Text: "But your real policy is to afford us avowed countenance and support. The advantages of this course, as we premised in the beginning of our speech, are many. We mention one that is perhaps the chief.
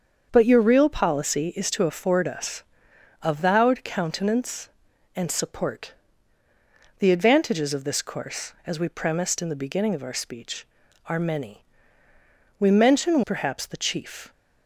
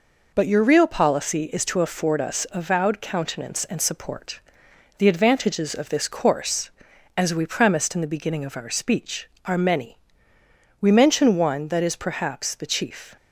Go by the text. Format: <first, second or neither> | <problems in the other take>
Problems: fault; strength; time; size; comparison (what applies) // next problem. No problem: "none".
second | starts louder than the rest; until 1.3 s; 7 dB // pauses between "us" and "avowed"; noticeable; at 2.6 s; 0.62 s long // skips "one that is"; at 13.2 s